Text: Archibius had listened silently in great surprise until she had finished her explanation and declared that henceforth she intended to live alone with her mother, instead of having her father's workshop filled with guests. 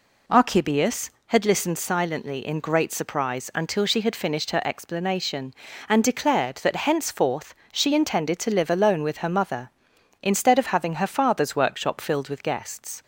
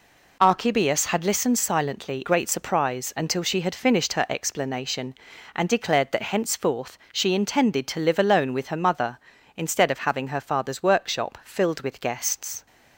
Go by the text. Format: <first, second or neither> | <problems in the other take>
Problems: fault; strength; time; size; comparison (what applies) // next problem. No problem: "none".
first | skips "in"; at 2.2 s // pauses between "henceforth" and "she"; slight; at 6.9 s; 0.16 s long; slight in the first